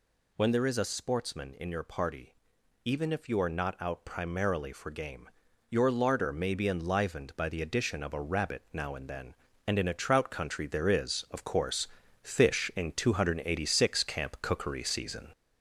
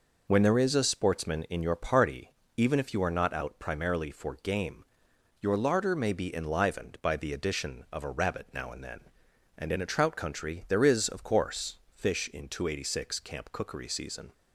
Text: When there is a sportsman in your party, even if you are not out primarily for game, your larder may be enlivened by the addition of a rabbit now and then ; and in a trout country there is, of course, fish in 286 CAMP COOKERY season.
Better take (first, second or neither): second